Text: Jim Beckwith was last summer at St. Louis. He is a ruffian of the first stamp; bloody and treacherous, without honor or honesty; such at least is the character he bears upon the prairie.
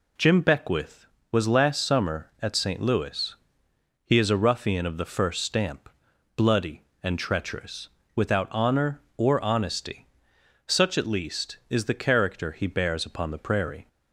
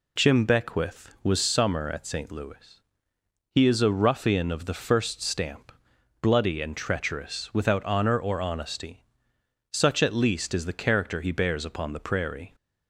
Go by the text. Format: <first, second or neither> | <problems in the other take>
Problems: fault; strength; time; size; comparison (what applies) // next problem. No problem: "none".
first | skips "last"; at 1.3 s